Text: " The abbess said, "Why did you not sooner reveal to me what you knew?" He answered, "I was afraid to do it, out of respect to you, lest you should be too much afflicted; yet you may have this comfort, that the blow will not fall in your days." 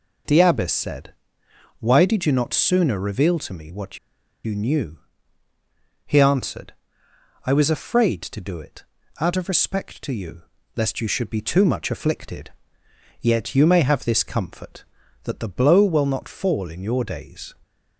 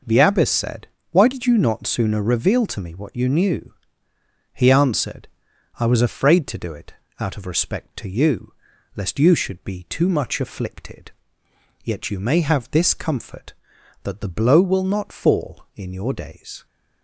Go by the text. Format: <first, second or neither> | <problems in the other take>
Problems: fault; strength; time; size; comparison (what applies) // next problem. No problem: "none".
second | pauses between "what" and "you"; noticeable; at 3.9 s; 0.47 s long